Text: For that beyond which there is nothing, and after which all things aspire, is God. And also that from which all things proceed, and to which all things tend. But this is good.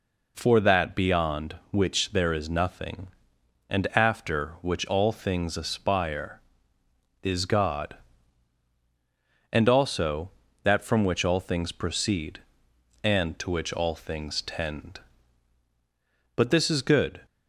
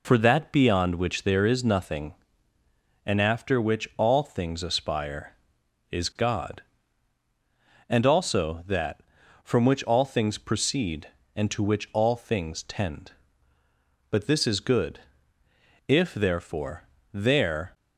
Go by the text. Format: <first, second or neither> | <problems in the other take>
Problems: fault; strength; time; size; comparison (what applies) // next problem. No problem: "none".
first | goes on to say "If therefore there"; strong; from 15.8 s on; 1.8 s long